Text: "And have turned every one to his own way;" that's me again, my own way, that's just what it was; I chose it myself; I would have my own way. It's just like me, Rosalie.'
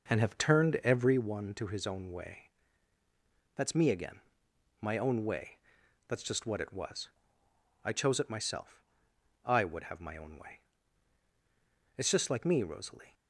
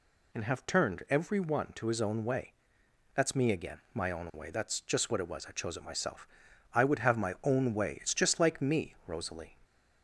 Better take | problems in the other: second | starts louder than the rest; noticeable; until 1.3 s; 6 dB

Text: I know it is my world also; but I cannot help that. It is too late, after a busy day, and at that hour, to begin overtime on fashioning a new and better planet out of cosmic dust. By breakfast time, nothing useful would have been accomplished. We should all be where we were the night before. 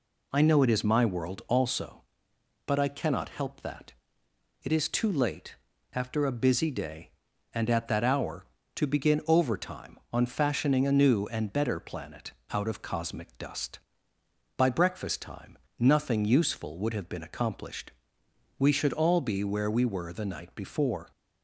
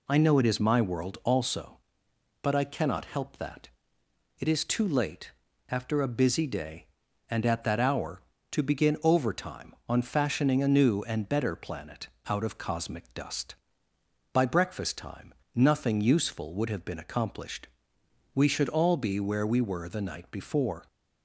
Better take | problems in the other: neither | pauses between "planet" and "out"; slight; the same in both

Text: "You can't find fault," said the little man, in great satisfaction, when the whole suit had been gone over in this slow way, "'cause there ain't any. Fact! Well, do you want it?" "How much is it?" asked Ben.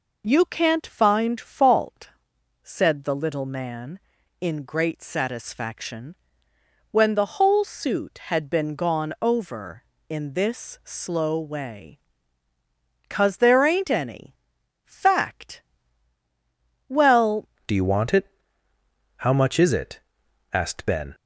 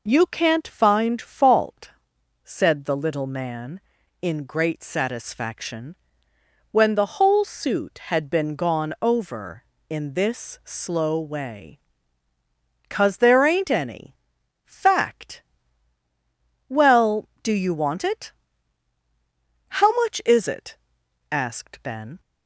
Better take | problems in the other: second | changes voice at "do"; from 17.6 s on; 3.5 s long

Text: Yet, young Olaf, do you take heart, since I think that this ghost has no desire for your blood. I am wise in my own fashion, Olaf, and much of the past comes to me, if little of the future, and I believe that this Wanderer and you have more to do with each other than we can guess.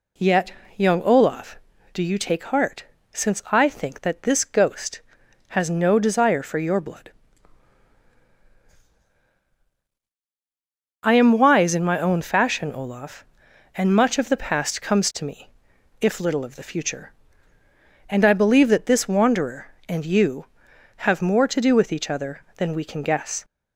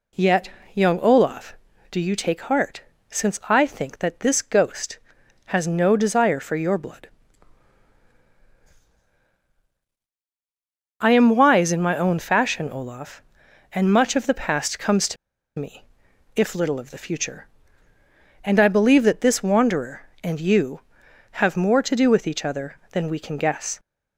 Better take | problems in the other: first | pauses between "to" and "me"; at 15.1 s; 0.43 s long

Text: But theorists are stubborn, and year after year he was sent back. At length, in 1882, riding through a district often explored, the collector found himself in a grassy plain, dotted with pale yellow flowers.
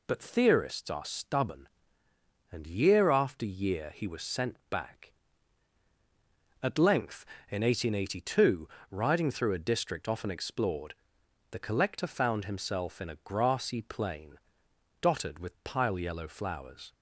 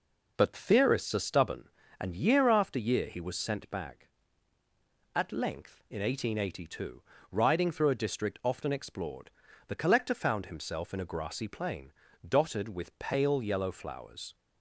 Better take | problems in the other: second | says "pile" for "pale"; at 15.6 s

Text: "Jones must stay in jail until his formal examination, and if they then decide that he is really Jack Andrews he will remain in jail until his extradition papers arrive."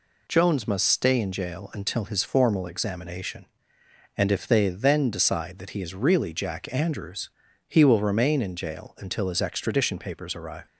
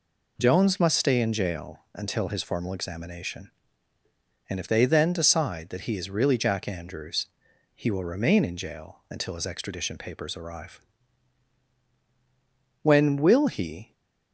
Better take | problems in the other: first | pauses between "Andrews" and "he"; noticeable; at 7.2 s; 0.50 s long; slight in the first // goes on to say "When will he"; noticeable; from 12.8 s on; 1.1 s long

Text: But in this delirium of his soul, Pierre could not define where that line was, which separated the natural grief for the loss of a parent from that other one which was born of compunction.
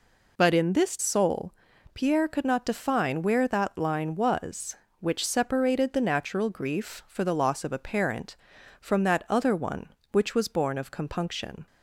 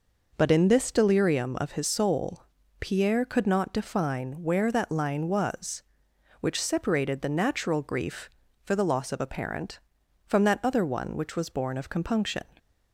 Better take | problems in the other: second | skips "delirium of his"; at 0.9 s

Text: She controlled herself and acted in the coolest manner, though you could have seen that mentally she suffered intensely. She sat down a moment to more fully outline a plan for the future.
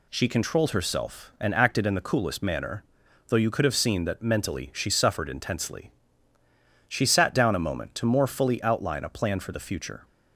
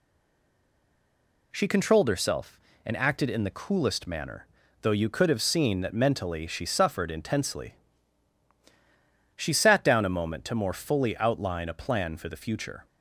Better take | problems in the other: first | stays silent before the first word; noticeable; until 1.5 s; 1.5 s long

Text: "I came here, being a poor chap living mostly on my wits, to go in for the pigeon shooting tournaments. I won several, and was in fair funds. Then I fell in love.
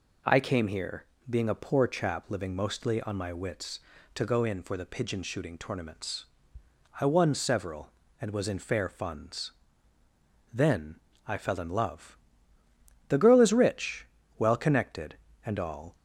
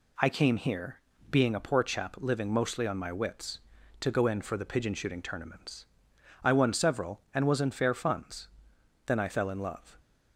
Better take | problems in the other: second | pauses between "Then" and "I"; slight; at 10.9 s; 0.28 s long // goes on to say "The girl is rich well connected and all"; strong; from 13.0 s on; 2.8 s long

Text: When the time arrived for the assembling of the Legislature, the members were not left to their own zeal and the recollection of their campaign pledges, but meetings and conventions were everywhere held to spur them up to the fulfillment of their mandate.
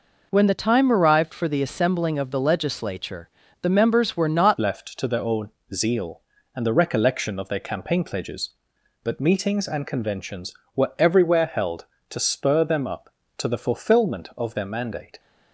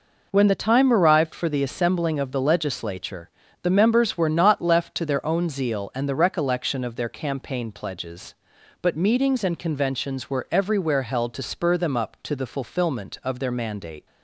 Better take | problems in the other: second | changes voice at "left"; from 4.5 s on; 10.6 s long // pauses between "own" and "zeal"; slight; at 5.4 s; 0.24 s long

